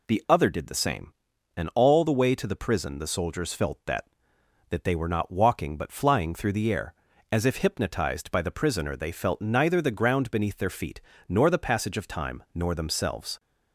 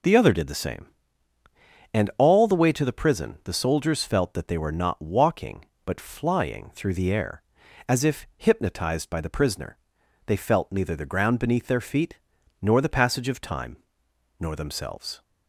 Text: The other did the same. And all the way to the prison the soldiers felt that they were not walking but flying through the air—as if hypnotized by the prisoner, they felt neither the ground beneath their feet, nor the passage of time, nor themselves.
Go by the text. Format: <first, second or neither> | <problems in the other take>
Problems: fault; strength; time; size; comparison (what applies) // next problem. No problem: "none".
second | says "that" twice; at 4.6 s